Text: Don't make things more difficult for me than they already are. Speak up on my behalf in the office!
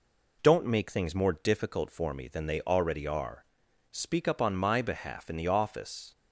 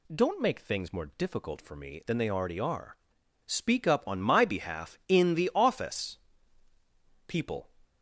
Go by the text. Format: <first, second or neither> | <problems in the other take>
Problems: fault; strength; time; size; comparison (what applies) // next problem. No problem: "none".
first | goes on to say "People"; slight; from 7.2 s on; 0.42 s long